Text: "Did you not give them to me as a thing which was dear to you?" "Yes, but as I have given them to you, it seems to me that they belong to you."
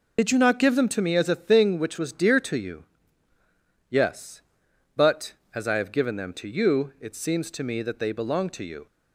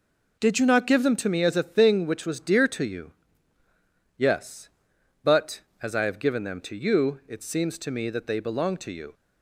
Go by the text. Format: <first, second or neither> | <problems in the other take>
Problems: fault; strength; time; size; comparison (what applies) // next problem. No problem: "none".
second | loses the start of "Did"; at 0.1 s; 65 ms